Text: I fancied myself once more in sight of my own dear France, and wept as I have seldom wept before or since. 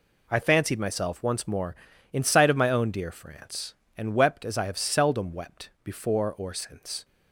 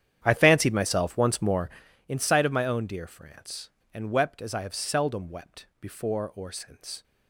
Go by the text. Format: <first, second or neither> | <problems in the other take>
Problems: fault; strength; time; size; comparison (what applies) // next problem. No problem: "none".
first | starts louder than the rest; strong; until 1.9 s; 10 dB